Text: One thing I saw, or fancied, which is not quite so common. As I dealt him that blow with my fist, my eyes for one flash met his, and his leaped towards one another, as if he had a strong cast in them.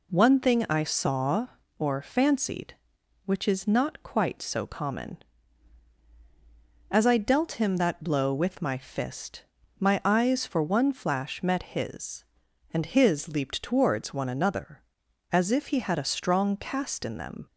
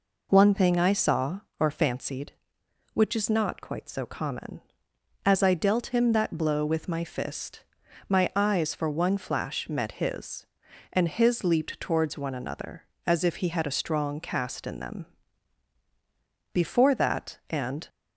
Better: first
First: none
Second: goes on to say "Before that and"; from 16.5 s on; 1.3 s long

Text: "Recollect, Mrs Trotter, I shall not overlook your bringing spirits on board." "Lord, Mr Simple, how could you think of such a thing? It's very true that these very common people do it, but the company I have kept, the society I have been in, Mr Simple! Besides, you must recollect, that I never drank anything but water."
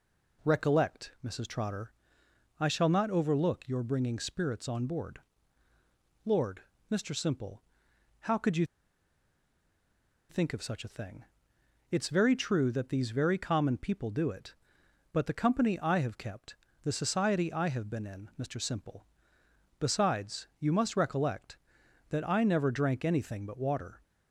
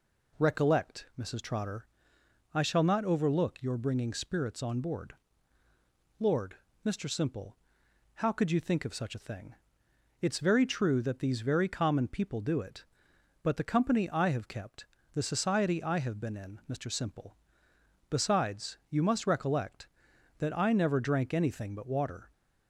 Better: second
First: pauses between "you" and "think"; strong; at 8.6 s; 1.6 s long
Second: none

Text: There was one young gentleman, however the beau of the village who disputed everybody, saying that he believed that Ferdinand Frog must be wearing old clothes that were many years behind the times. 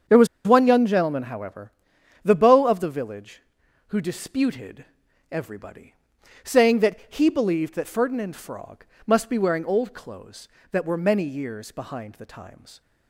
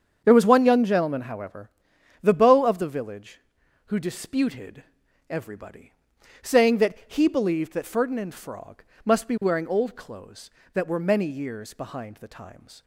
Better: second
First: starts louder than the rest; strong; until 1.2 s; 7.5 dB // pauses between "was" and "one"; slight; at 0.2 s; 0.19 s long // pauses between "however" and "the"; noticeable; at 1.7 s; 0.52 s long // pauses between "disputed" and "everybody"; at 4.8 s; 0.44 s long // pauses between "Frog" and "must"; slight; at 8.8 s; 0.18 s long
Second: starts louder than the rest; strong; until 1.2 s; 7.5 dB // pauses between "however" and "the"; noticeable; at 1.6 s; 0.52 s long // pauses between "disputed" and "everybody"; at 4.8 s; 0.44 s long // pauses between "Frog" and "must"; slight; at 8.8 s; 0.18 s long

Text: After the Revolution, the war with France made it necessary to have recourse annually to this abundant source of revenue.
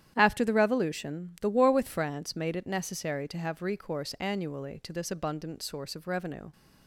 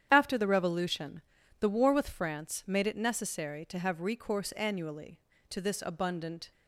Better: first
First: starts louder than the rest; strong; until 1.1 s; 10.5 dB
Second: starts louder than the rest; strong; until 1.1 s; 9.5 dB // stops before "source of revenue"; at 6.5 s

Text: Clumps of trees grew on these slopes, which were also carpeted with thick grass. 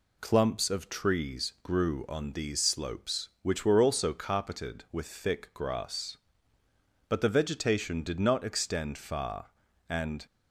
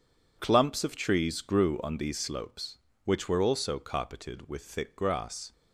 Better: second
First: goes on to say "But the vegetation did not extend far and"; strong; from 7.0 s on; 3.1 s long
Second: none

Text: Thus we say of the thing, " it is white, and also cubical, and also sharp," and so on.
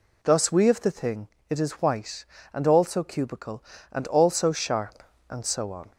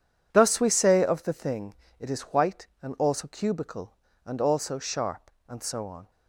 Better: second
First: skips "say"; at 0.6 s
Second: none

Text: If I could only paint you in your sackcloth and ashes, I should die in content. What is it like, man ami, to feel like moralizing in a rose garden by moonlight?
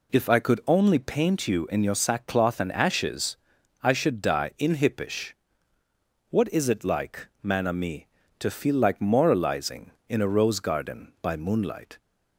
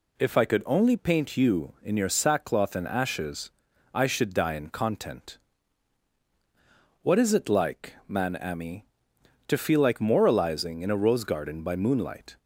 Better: second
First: says "hippish" for "content"; at 4.7 s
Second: none

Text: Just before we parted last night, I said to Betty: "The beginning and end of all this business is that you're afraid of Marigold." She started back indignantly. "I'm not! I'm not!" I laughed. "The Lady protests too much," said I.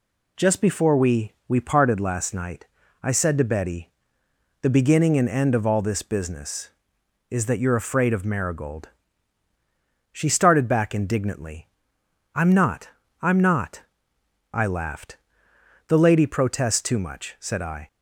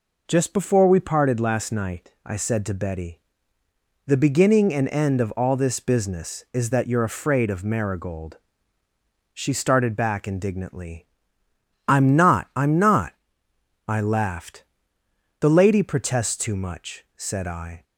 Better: second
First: says "we" twice; at 1.4 s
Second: none

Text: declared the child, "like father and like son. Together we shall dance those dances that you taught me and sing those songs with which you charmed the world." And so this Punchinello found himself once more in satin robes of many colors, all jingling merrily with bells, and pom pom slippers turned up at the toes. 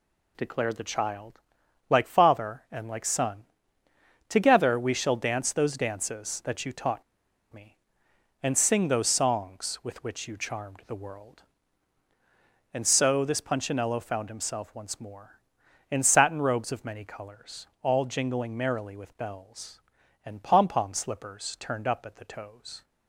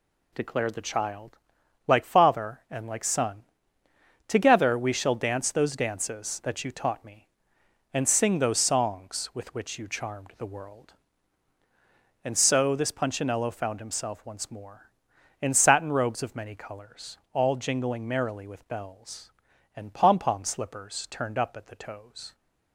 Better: second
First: pauses between "taught" and "me"; noticeable; at 7.0 s; 0.51 s long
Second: none

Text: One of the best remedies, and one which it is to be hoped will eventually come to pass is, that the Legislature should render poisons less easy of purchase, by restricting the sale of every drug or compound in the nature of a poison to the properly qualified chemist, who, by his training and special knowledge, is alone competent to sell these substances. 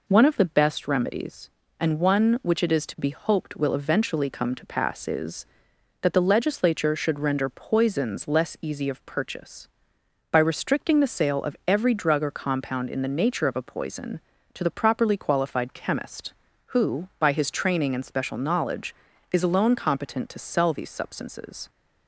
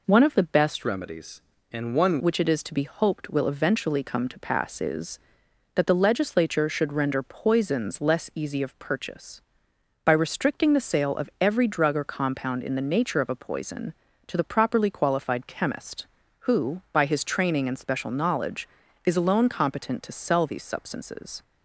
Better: first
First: none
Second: changes voice from "remedies" to "one"; from 0.8 to 2.1 s; 1.3 s long

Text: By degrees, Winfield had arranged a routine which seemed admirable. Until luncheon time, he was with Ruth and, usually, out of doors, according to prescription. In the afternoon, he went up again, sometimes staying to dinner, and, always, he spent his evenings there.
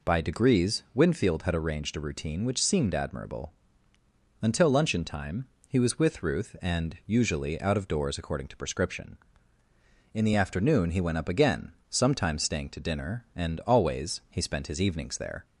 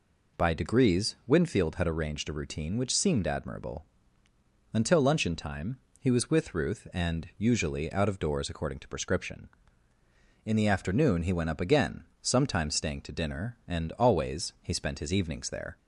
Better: neither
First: none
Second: none

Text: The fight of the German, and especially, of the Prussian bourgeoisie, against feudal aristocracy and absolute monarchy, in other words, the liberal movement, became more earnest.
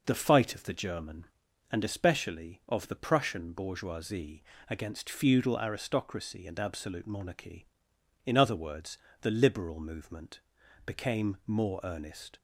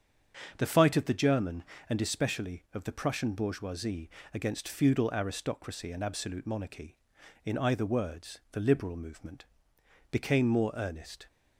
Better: first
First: none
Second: starts louder than the rest; strong; until 1.5 s; 7 dB // says "either" for "other"; at 7.5 s

